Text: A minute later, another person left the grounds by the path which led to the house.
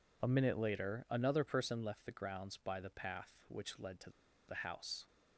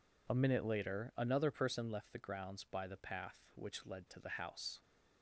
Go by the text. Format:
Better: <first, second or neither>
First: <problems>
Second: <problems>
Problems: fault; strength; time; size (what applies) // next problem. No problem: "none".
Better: second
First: pauses between "to" and "the"; at 4.1 s; 0.36 s long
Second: none